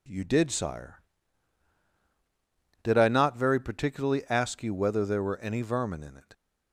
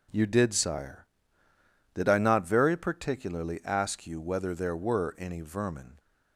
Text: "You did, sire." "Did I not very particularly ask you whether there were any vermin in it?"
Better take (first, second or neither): first